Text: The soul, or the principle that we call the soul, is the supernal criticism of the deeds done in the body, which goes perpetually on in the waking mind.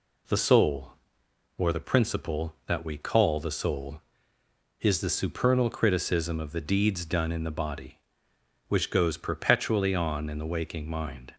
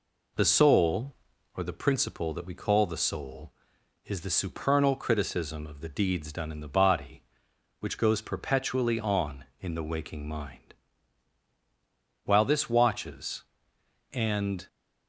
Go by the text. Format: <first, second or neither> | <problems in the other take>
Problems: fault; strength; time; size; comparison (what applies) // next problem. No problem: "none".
first | goes on to say "While this watches and"; strong; from 12.2 s on; 2.4 s long